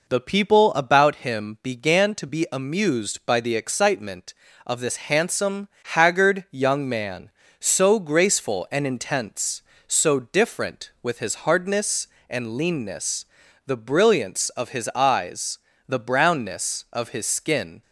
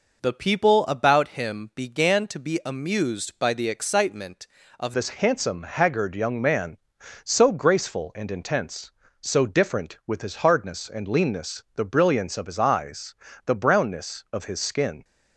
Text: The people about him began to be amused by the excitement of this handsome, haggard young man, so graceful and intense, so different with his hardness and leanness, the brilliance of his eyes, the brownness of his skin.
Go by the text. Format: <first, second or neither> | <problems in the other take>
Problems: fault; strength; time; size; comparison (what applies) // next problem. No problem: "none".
first | changes voice at "this"; from 4.9 s on; 10.1 s long